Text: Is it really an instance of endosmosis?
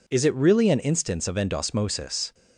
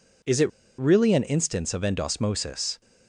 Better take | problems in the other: first | pauses between "it" and "really"; slight; at 0.4 s; 0.30 s long

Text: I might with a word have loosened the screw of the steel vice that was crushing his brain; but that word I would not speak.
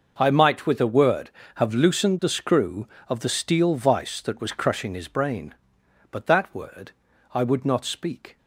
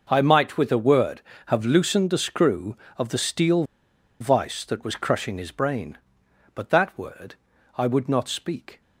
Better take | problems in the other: first | pauses between "steel" and "vice"; noticeable; at 3.6 s; 0.56 s long // pauses between "word" and "I"; at 7.3 s; 0.42 s long; also in the first

